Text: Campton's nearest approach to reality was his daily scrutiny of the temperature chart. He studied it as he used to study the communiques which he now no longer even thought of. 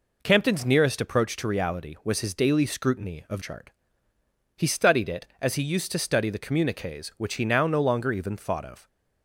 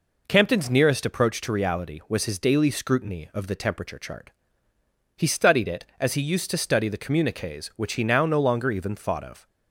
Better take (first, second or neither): second